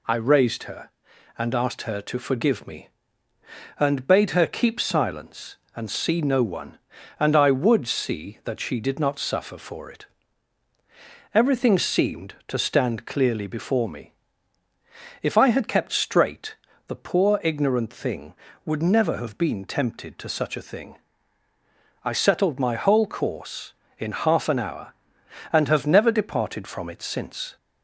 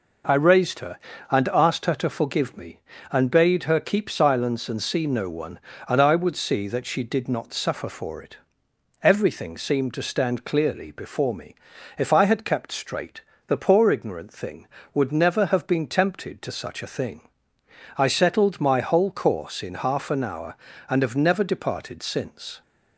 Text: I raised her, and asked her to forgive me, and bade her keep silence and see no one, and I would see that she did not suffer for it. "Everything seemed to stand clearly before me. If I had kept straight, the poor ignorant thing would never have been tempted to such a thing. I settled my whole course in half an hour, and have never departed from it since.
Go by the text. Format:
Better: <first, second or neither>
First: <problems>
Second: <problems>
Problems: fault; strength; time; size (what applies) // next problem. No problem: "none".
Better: first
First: none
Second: skips "from it"; at 22.0 s